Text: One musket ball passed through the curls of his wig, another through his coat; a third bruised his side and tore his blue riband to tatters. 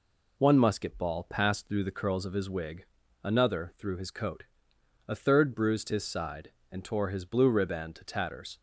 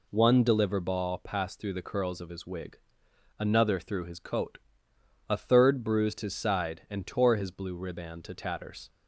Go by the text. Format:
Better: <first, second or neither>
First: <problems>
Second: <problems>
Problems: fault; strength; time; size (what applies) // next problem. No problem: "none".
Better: first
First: none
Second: says "deliver" for "musket"; at 0.4 s